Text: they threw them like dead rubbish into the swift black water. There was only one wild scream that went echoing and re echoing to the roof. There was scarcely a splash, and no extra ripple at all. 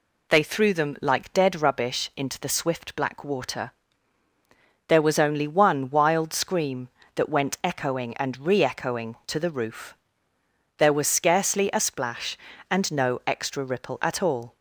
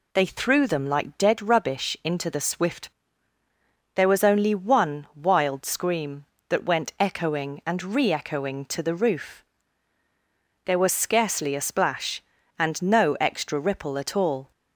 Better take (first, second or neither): first